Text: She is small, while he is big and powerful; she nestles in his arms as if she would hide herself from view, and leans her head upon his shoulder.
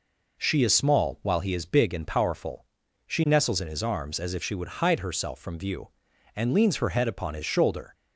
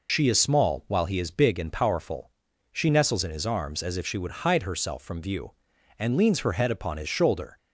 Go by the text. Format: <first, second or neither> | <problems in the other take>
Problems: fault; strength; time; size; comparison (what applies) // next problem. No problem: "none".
first | loses the start of "She"; at 0.0 s; 45 ms